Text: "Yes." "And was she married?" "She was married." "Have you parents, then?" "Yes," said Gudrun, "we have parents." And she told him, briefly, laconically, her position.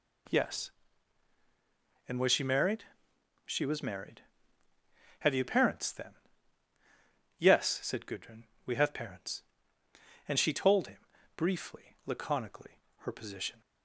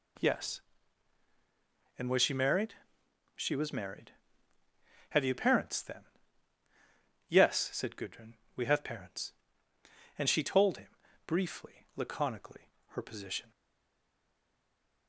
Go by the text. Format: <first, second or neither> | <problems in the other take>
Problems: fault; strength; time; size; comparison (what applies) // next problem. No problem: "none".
first | stays silent after the last word; noticeable; from 13.5 s on; 1.5 s long